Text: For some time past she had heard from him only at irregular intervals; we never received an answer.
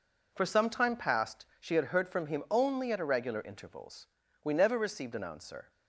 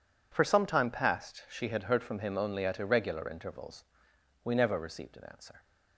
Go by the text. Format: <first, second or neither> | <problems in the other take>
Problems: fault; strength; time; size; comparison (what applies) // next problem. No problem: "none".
neither | none